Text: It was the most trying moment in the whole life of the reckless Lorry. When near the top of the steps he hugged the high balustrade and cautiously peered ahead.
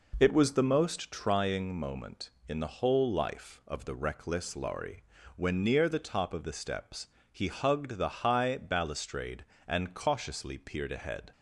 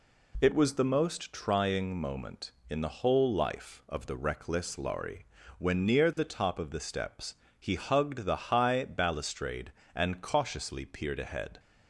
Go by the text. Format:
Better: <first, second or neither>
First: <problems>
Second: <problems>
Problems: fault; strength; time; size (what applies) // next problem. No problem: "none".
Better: second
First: starts louder than the rest; noticeable; until 1.4 s; 4 dB // pauses between "steps" and "he"; slight; at 7.0 s; 0.24 s long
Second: pauses between "steps" and "he"; slight; at 7.3 s; 0.24 s long